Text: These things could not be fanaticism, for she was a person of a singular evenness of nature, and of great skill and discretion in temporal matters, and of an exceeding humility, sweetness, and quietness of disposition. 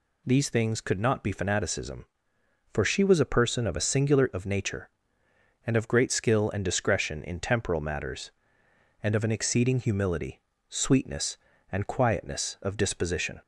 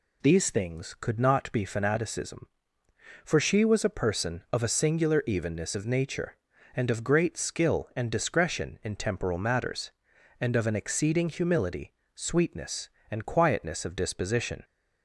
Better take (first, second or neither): second